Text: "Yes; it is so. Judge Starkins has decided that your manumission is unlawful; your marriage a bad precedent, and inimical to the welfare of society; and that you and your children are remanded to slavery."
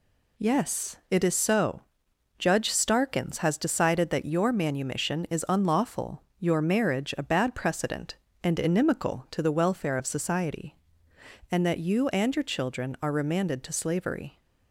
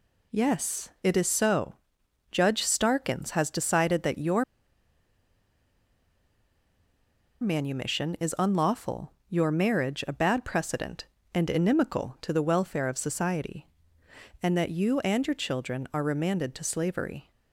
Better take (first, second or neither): first